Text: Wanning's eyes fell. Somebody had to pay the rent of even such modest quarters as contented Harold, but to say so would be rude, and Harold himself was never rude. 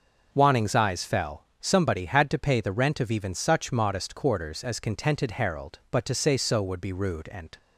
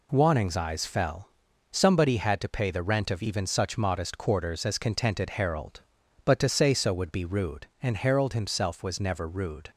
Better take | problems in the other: second | stops before "Harold himself was never rude"; at 7.5 s

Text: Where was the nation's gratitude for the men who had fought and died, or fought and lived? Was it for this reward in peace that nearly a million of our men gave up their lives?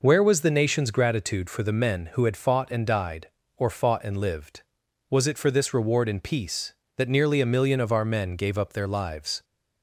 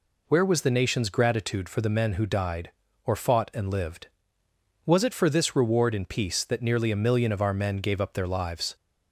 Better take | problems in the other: first | skips "had fought and"; at 2.2 s

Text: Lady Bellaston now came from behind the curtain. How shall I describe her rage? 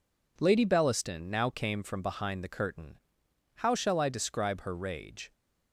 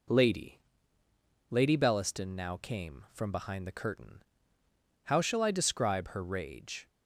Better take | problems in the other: first | says "Lady" twice; at 1.5 s

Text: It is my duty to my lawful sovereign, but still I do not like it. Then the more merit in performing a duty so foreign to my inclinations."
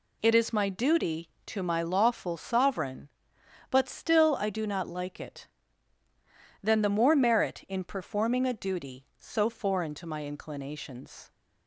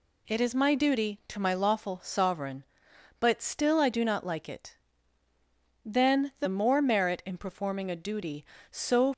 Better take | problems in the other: first | stops before "foreign to my inclinations"; at 9.1 s

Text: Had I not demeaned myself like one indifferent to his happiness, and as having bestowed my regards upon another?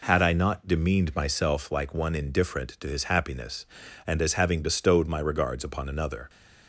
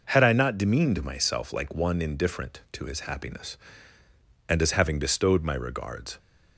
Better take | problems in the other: first | stops before "upon another"; at 6.1 s

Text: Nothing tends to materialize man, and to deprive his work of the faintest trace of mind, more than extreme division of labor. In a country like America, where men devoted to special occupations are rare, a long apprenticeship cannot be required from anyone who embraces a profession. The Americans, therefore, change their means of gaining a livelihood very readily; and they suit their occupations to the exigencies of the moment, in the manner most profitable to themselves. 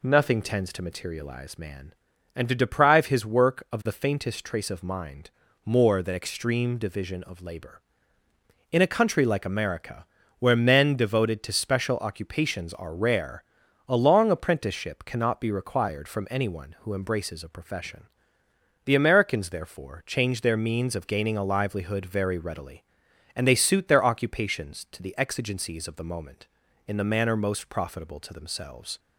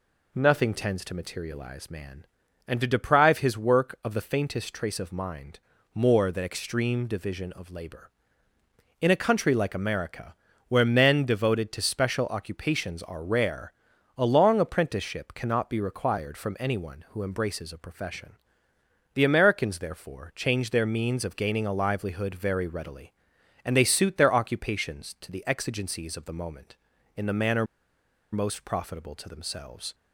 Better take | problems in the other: first | pauses between "manner" and "most"; noticeable; at 27.6 s; 0.68 s long

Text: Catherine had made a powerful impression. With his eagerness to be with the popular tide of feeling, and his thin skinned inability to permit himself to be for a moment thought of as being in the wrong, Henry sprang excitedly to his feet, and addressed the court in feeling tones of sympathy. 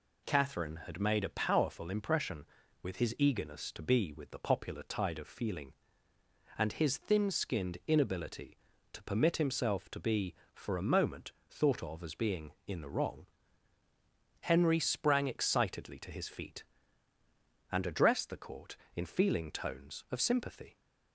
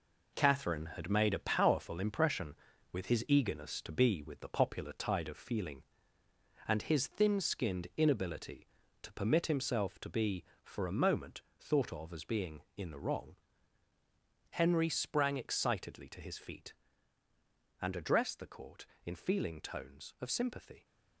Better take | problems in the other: first | gets quieter; strong; throughout; 7 dB // pauses between "moment" and "thought"; slight; at 11.4 s; 0.18 s long; slight in the first

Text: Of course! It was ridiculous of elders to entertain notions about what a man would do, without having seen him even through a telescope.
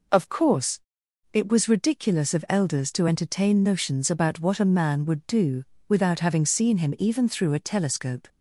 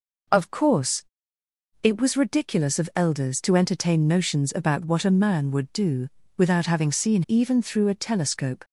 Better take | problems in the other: first | skips "him"; at 7.2 s

